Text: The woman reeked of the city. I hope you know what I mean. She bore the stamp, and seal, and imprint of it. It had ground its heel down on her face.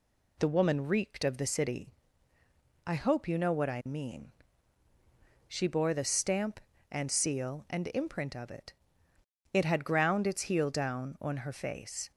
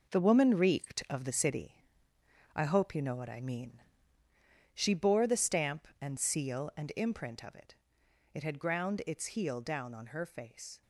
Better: first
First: none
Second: gets quieter; strong; throughout; 9 dB

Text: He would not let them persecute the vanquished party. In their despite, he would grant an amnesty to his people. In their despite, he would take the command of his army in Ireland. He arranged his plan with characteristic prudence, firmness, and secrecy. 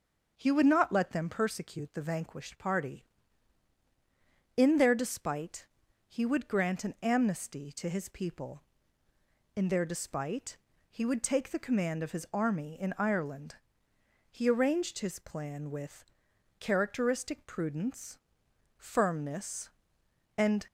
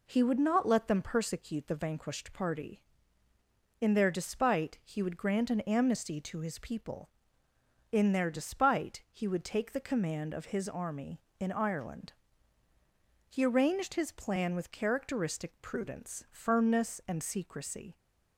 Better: second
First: starts louder than the rest; noticeable; until 1.3 s; 6 dB // pauses between "with" and "characteristic"; noticeable; at 16.0 s; 0.54 s long // stops before "secrecy"; at 20.6 s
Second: none

